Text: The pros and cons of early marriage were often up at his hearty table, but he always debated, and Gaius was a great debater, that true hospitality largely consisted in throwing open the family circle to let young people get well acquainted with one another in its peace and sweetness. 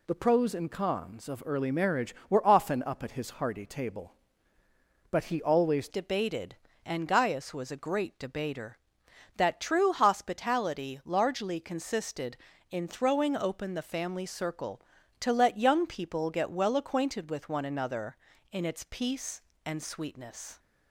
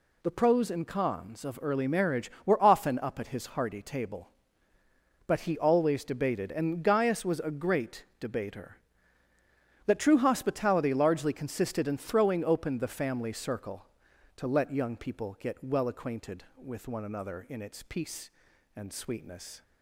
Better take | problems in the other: second | changes voice at "debated"; from 5.8 s on; 14.7 s long

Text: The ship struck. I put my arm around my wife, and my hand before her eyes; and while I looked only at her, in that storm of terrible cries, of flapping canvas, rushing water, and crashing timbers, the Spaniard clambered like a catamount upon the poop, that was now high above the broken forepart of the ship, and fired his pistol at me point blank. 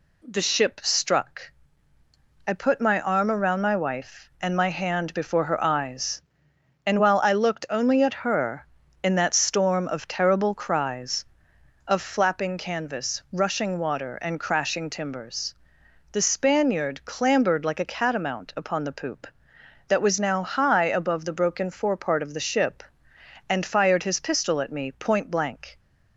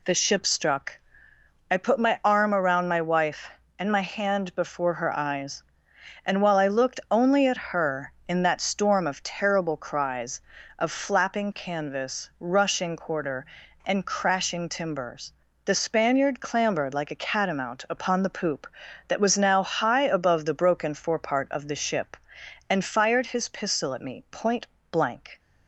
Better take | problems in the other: first | says "quarter" for "water"; at 12.9 s // pauses between "point" and "blank"; slight; at 24.6 s; 0.24 s long

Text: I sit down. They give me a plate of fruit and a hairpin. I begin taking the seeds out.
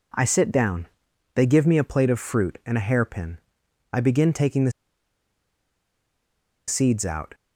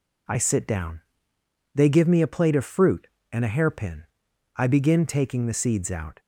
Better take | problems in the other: second | pauses between "the" and "seeds"; strong; at 4.7 s; 1.9 s long

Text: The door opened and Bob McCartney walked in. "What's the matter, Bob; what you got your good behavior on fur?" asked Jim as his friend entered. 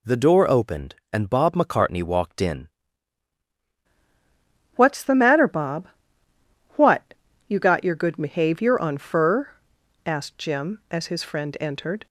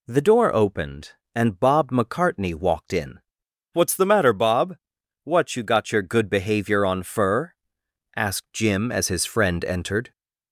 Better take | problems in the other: second | changes voice at "What's"; from 4.7 s on; 7.3 s long // pauses between "what" and "you"; slight; at 7.1 s; 0.34 s long

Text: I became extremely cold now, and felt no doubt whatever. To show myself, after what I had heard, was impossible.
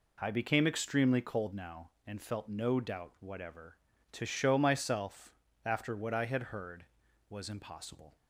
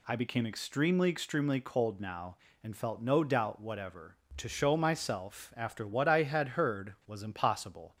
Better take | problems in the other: first | says "extremely" twice; at 1.0 s

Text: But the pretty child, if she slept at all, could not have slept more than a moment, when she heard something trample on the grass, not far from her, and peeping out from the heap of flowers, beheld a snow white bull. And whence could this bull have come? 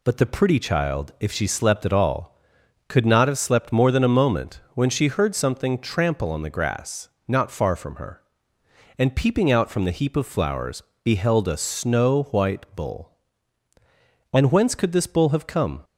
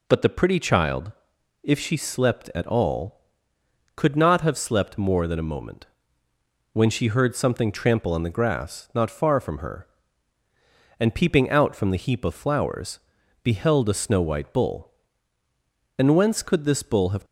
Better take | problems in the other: first | stops before "come"; at 17.2 s

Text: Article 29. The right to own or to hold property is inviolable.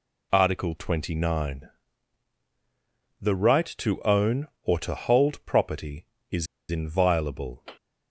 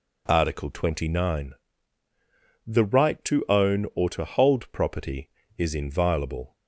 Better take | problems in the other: second | pauses between "is" and "inviolable"; slight; at 6.4 s; 0.25 s long

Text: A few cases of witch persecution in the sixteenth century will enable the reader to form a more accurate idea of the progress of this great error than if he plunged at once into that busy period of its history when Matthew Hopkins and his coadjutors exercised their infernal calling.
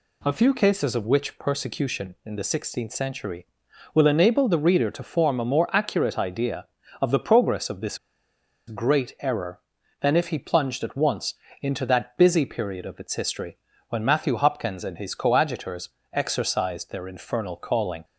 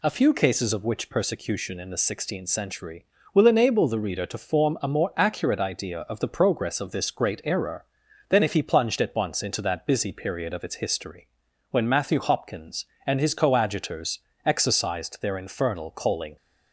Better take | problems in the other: second | pauses between "this" and "great"; noticeable; at 7.9 s; 0.69 s long // pauses between "once" and "into"; slight; at 11.3 s; 0.28 s long // pauses between "history" and "when"; slight; at 13.5 s; 0.32 s long; also in the second // pauses between "coadjutors" and "exercised"; slight; at 15.8 s; 0.24 s long; slight in the second

